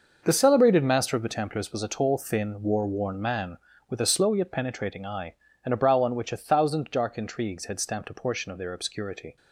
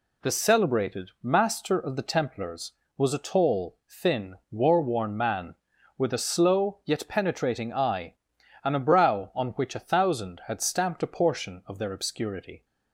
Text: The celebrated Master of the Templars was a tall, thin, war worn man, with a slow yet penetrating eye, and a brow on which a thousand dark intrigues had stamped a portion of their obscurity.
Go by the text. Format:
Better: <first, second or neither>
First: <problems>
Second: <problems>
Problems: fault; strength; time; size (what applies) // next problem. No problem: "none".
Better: first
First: none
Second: skips "dark intrigues"; at 10.4 s